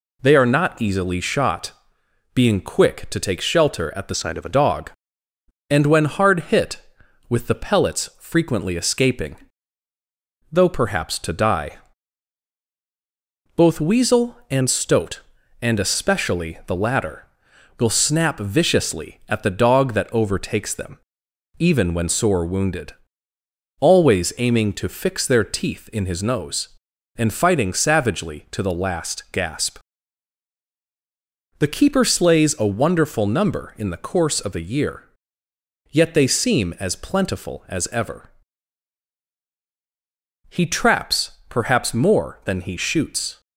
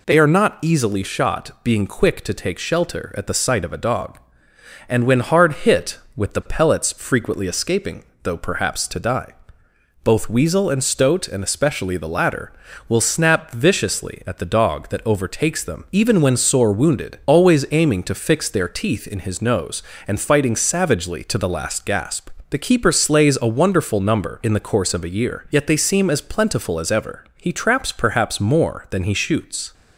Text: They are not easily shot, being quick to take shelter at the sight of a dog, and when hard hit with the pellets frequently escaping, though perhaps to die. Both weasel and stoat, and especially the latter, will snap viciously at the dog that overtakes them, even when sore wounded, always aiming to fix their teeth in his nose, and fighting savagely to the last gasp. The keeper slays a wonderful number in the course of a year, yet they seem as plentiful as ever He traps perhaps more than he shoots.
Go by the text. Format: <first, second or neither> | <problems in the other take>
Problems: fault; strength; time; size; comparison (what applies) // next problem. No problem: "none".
second | changes voice from "sight" to "a"; from 4.1 to 4.5 s; 0.4 s long // pauses between "ever" and "He"; strong; at 38.2 s; 2.2 s long